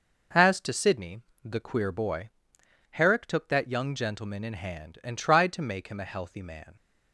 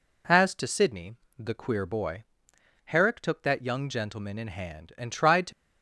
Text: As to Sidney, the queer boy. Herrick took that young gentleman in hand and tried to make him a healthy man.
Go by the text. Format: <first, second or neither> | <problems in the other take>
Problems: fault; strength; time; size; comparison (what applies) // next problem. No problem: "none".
first | stops before "make him a healthy man"; at 5.5 s